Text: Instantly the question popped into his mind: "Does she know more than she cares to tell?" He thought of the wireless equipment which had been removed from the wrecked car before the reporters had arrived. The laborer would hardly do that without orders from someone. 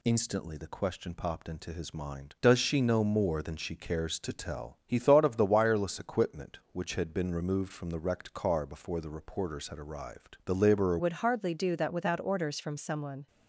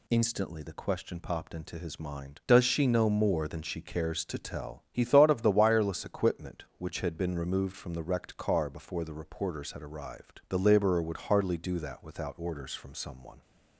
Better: second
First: changes voice at "would"; from 10.9 s on; 2.3 s long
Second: none

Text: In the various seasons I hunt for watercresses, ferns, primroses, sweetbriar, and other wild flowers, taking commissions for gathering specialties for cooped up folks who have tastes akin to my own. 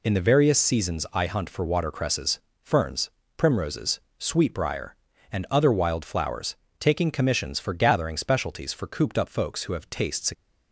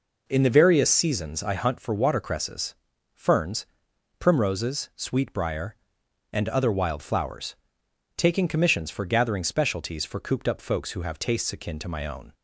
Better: second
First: stops before "akin to my own"; at 10.3 s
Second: none

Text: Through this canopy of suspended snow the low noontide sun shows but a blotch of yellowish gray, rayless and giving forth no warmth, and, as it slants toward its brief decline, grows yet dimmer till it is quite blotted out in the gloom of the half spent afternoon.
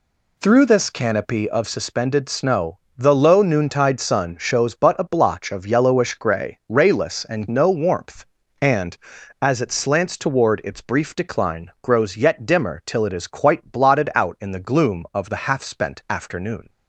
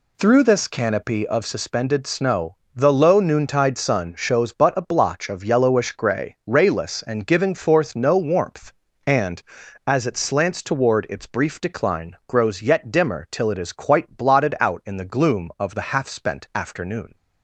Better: second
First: pauses between "snow" and "the"; slight; at 2.7 s; 0.18 s long // skips "giving forth"; at 7.4 s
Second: pauses between "snow" and "the"; slight; at 2.5 s; 0.18 s long

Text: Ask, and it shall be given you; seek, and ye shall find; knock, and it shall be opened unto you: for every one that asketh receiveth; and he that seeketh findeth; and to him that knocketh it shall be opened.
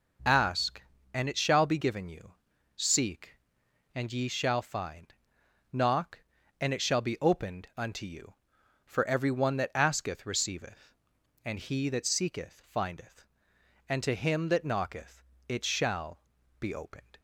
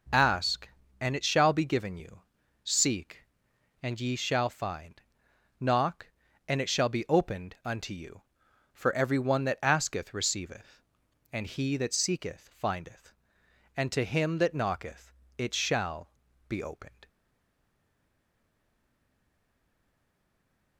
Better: first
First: pauses between "knocketh" and "it"; slight; at 15.2 s; 0.26 s long // pauses between "shall" and "be"; at 16.1 s; 0.40 s long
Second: pauses between "knocketh" and "it"; slight; at 15.1 s; 0.26 s long // pauses between "shall" and "be"; at 16.0 s; 0.38 s long // stays silent after the last word; strong; from 17.0 s on; 3.7 s long

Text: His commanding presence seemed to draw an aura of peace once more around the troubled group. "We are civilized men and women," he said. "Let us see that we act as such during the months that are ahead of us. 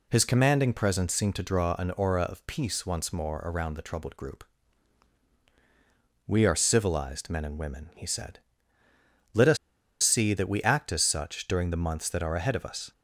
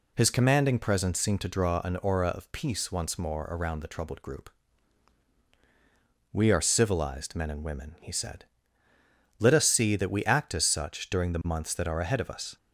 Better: second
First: pauses between "us" and "see"; noticeable; at 9.5 s; 0.46 s long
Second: none

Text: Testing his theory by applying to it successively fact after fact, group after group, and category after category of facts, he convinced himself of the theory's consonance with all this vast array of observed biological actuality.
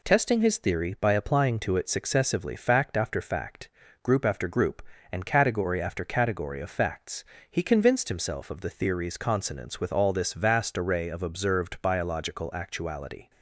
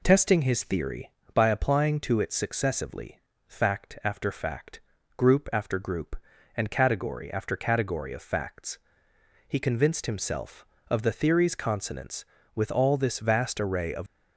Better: first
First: none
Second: pauses between "successively" and "fact"; slight; at 3.2 s; 0.26 s long // stops before "observed biological actuality"; at 14.0 s

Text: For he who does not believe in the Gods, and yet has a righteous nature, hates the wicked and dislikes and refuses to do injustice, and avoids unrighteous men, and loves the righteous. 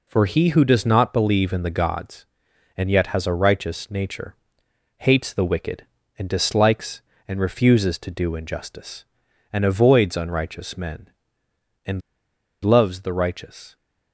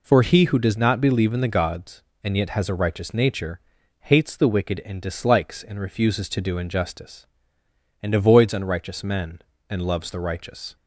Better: second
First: pauses between "and" and "loves"; noticeable; at 12.0 s; 0.62 s long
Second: none

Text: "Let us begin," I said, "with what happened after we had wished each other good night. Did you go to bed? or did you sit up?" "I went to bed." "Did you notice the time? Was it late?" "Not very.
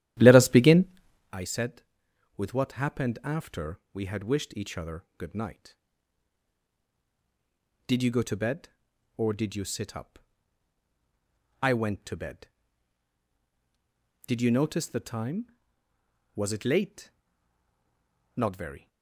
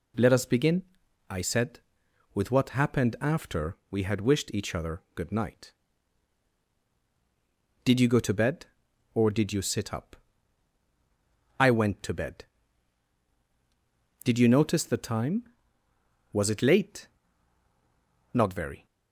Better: second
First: starts louder than the rest; strong; until 1.4 s; 12.5 dB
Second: none

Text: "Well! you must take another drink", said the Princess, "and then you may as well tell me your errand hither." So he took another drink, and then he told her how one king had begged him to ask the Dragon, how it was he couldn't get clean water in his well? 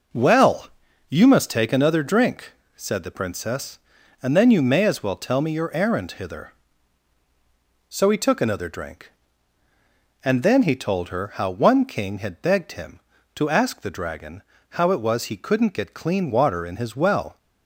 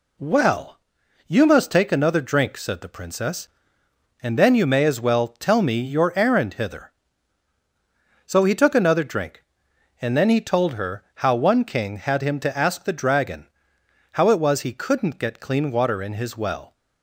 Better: first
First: none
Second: skips "begged"; at 12.2 s

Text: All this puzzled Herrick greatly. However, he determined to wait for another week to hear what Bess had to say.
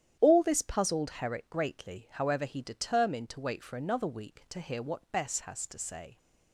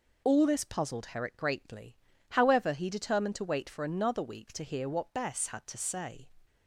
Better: second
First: starts louder than the rest; strong; until 1.2 s; 10.5 dB // says "has" for "had"; at 5.4 s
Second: none

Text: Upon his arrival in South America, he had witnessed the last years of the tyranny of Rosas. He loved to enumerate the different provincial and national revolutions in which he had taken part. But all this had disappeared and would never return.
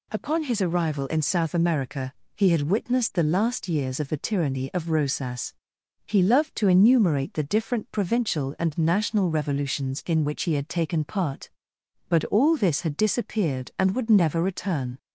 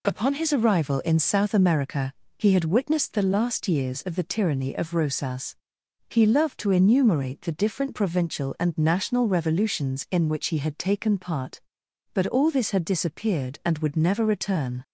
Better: neither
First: none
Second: none

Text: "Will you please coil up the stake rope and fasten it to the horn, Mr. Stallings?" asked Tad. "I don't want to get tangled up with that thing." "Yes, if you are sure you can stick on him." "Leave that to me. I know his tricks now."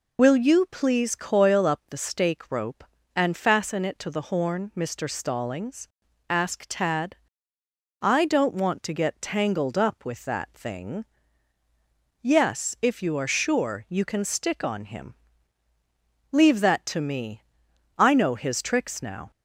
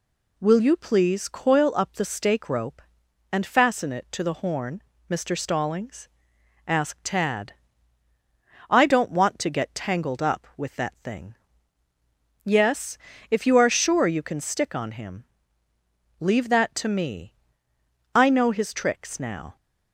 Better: second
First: loses the start of "Will"; at 0.1 s; 60 ms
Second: none

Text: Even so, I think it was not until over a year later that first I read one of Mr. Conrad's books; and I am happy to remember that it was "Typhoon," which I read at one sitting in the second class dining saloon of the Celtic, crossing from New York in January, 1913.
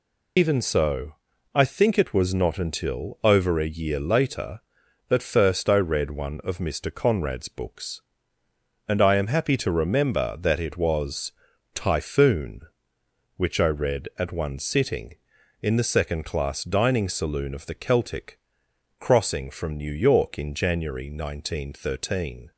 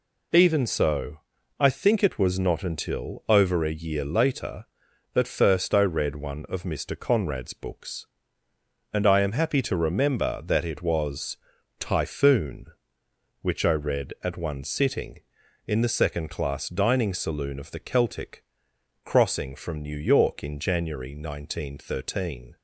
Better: second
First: loses the start of "Even"; at 0.3 s; 90 ms // pauses between "was" and "Typhoon"; at 11.3 s; 0.42 s long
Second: pauses between "was" and "Typhoon"; at 11.3 s; 0.42 s long

